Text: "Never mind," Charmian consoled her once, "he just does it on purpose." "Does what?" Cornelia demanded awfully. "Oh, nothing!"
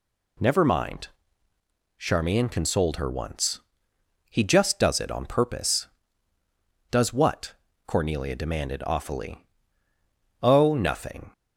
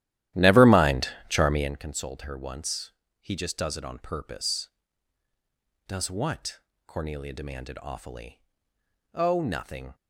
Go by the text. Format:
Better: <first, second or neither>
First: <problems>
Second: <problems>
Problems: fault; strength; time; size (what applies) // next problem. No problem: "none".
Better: first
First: none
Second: starts louder than the rest; strong; until 1.8 s; 13 dB